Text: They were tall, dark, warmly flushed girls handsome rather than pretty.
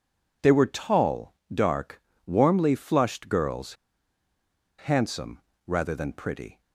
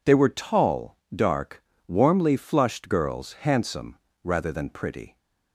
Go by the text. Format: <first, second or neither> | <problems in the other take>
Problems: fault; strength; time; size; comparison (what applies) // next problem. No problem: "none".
second | pauses between "girls" and "handsome"; at 3.7 s; 1.0 s long // pauses between "handsome" and "rather"; slight; at 5.3 s; 0.26 s long; slight in the second